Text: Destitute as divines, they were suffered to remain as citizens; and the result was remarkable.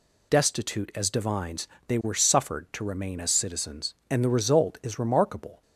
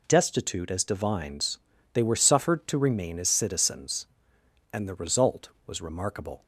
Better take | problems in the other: second | says "is" for "was"; at 4.8 s

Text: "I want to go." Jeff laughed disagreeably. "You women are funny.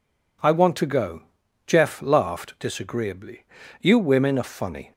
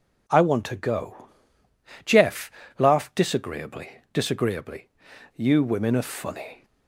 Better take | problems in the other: first | pauses between "Jeff" and "laughed"; slight; at 2.5 s; 0.28 s long // says "disagreeably" twice; at 4.1 s

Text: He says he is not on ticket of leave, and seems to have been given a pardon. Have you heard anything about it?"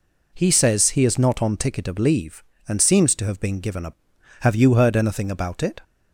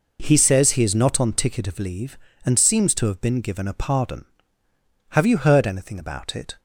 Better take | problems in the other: second | skips "pardon"; at 4.1 s

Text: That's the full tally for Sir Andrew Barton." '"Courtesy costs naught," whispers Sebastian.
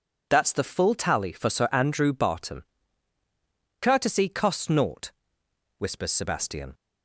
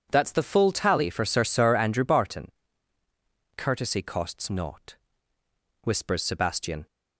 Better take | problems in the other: first | says "Sir" twice; at 1.4 s

